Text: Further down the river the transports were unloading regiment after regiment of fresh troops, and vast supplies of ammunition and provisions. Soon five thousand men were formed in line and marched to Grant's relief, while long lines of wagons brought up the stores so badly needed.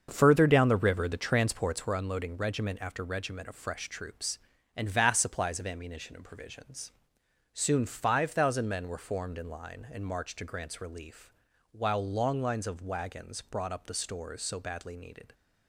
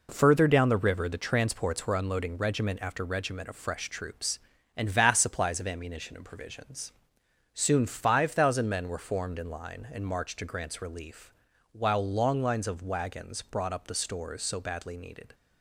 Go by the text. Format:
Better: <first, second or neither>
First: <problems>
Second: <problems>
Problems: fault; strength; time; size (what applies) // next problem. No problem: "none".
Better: second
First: starts louder than the rest; until 1.9 s; 6.5 dB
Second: none